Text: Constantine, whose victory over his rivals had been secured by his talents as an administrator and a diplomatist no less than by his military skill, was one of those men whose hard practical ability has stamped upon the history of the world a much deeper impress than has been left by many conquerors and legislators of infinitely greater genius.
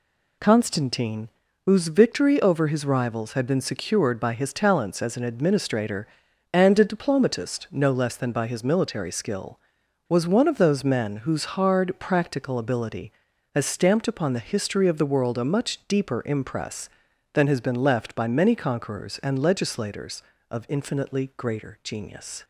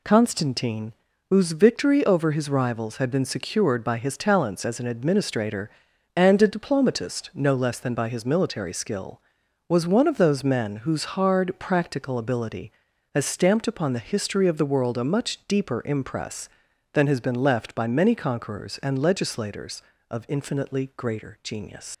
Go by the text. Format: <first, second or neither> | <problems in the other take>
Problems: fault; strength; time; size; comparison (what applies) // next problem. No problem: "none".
first | leaves "genius" unfinished; at 21.9 s; 90 ms